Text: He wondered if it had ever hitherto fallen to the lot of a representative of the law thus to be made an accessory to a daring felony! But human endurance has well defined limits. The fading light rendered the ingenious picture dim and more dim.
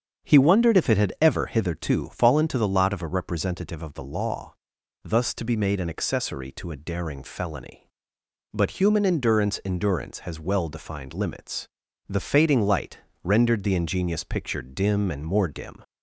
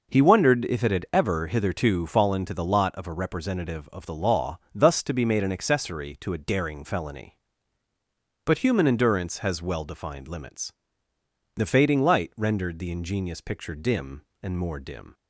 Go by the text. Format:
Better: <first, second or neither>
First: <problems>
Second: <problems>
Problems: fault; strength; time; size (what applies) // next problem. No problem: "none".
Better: second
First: starts louder than the rest; strong; until 1.3 s; 7.5 dB // pauses between "law" and "thus"; noticeable; at 4.5 s; 0.48 s long // says "endurance" twice; at 9.6 s // pauses between "light" and "rendered"; slight; at 12.9 s; 0.24 s long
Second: pauses between "law" and "thus"; slight; at 4.5 s; 0.16 s long